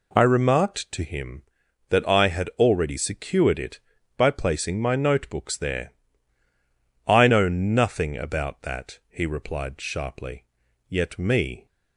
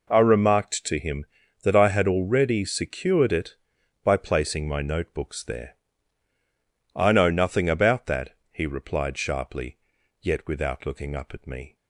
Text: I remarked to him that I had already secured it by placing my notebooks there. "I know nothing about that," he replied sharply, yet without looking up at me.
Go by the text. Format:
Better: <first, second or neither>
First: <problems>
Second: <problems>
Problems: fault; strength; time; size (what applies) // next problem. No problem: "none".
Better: second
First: skips "without looking up at"; at 11.1 s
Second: none